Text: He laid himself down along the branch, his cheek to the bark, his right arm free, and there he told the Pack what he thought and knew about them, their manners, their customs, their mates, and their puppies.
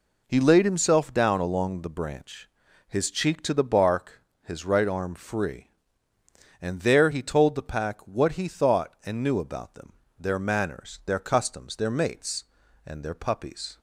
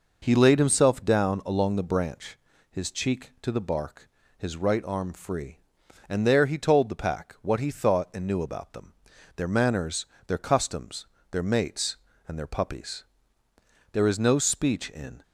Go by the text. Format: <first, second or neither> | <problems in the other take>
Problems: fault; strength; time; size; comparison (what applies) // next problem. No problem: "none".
first | goes on to say "There is no speech in"; noticeable; from 13.9 s on; 1.2 s long